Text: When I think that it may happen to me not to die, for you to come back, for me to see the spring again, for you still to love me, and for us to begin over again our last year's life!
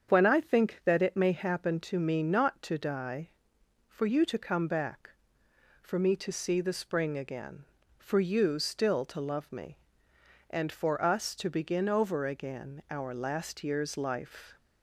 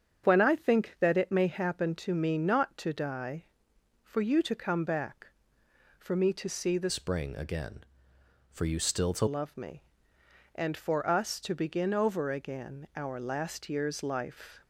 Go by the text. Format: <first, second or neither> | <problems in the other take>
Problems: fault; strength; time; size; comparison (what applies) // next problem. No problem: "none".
first | starts louder than the rest; strong; until 1.2 s; 8 dB; strong in the first // changes voice from "spring" to "to"; from 6.8 to 9.2 s; 2.4 s long